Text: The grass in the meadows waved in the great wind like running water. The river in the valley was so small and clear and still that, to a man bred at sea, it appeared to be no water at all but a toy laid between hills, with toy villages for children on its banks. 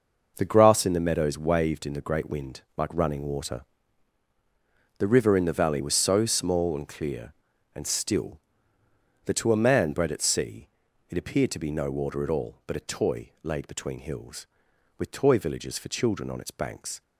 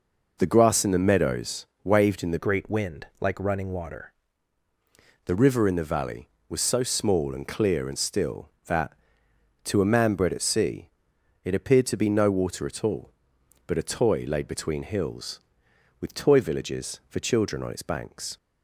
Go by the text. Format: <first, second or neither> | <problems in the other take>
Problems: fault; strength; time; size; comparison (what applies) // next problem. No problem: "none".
first | pauses between "meadows" and "waved"; slight; at 1.6 s; 0.18 s long // changes voice from "great" to "water"; from 2.3 to 4.1 s; 1.8 s long